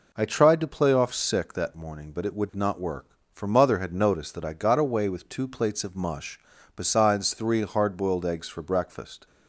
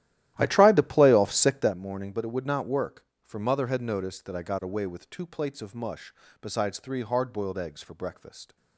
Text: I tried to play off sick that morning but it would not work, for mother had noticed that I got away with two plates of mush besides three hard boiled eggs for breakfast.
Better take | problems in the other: first | starts louder than the rest; strong; until 1.8 s; 13.5 dB // pauses between "mush" and "besides"; slight; at 6.1 s; 0.30 s long; slight in the first

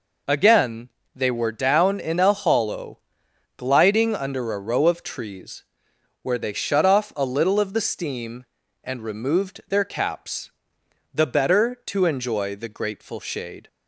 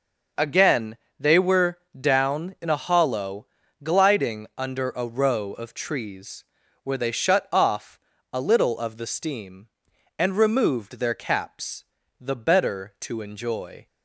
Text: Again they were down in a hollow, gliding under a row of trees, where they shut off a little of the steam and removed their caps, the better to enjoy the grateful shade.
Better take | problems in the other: first | pauses between "Again" and "they"; slight; at 0.9 s; 0.20 s long; slight in the first // pauses between "were" and "down"; slight; at 1.7 s; 0.20 s long // pauses between "off" and "a"; slight; at 7.9 s; 0.36 s long // stops before "the grateful shade"; at 13.8 s

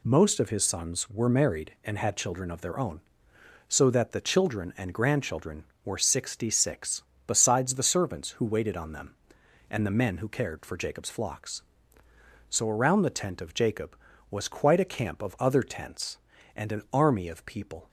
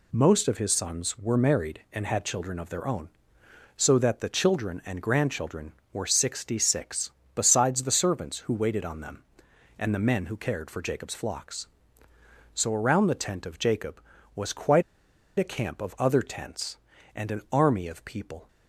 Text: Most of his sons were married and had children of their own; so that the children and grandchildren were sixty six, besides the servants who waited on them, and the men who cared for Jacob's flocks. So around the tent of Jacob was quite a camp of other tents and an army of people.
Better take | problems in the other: first | pauses between "quite" and "a"; noticeable; at 14.8 s; 0.54 s long

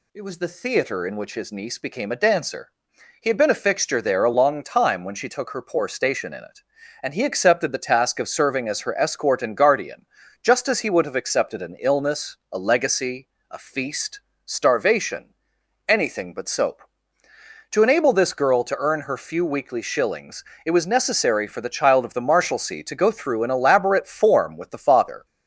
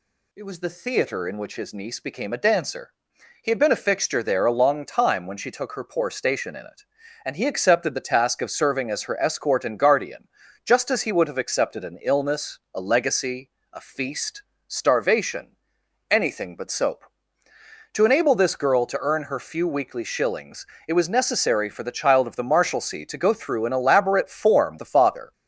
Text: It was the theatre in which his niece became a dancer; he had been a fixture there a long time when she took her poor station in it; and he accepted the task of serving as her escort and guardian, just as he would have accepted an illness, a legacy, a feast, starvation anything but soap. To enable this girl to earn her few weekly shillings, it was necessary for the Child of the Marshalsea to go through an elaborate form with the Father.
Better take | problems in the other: first | pauses between "starvation" and "anything"; noticeable; at 15.5 s; 0.52 s long; noticeable in the first // skips "with"; at 24.7 s

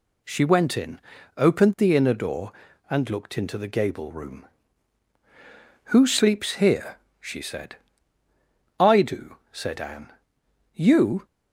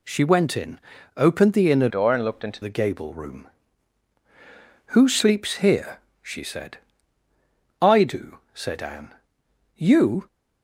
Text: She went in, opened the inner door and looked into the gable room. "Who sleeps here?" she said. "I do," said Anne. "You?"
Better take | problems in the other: first | changes voice from "door" to "into"; from 1.8 to 2.6 s; 0.8 s long

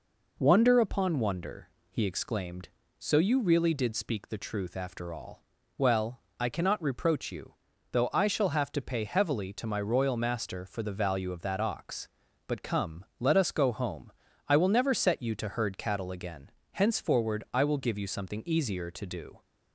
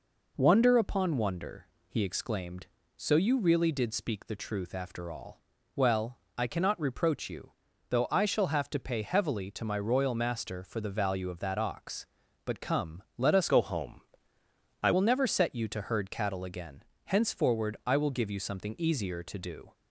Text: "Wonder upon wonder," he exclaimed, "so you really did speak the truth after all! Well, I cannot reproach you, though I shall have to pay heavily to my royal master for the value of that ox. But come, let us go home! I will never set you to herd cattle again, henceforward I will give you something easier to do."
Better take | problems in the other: first | changes voice from "go" to "I"; from 13.4 to 14.9 s; 1.5 s long

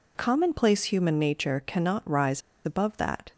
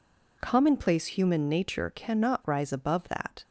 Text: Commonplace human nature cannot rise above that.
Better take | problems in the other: second | pauses between "rise" and "above"; slight; at 2.3 s; 0.24 s long

